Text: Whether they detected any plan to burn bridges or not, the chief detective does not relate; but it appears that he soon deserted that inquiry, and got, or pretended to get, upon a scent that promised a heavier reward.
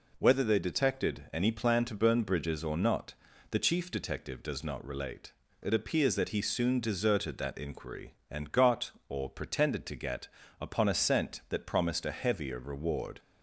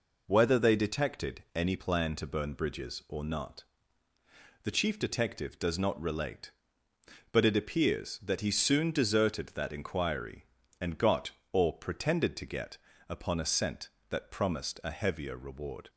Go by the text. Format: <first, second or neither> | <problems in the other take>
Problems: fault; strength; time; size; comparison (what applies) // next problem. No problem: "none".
second | skips "but"; at 5.4 s